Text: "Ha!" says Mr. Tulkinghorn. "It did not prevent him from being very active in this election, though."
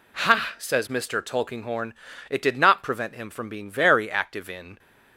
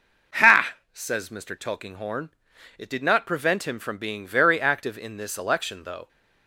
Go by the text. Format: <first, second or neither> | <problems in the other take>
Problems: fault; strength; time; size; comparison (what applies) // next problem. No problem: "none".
second | stops before "this election though"; at 4.7 s